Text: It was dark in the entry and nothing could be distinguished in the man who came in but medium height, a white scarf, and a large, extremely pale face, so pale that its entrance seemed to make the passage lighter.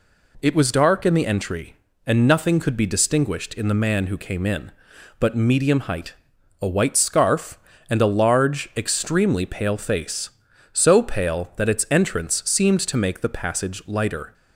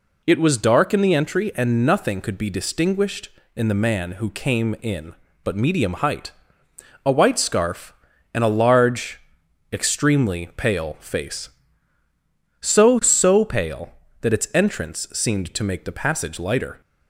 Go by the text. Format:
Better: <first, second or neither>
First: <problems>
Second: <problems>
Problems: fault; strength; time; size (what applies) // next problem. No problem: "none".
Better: first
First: none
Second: says "so" twice; at 13.0 s